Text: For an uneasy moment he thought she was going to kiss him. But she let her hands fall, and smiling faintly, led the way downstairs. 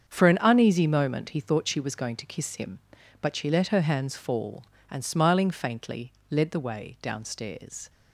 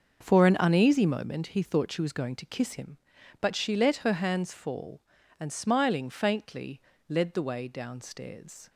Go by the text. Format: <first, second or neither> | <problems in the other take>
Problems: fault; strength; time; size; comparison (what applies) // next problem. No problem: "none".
neither | starts louder than the rest; the same in both